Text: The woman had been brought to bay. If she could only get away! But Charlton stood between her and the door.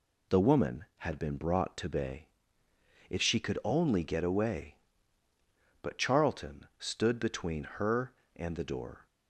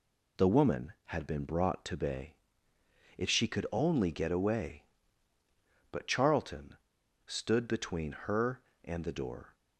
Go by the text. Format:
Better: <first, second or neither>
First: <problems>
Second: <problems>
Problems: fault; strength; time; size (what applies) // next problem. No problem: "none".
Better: first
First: none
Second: pauses between "Charlton" and "stood"; noticeable; at 6.7 s; 0.52 s long